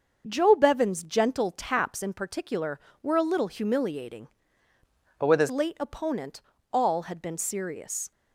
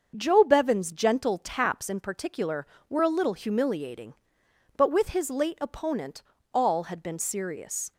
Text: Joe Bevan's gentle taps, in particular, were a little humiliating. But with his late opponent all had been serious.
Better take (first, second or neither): second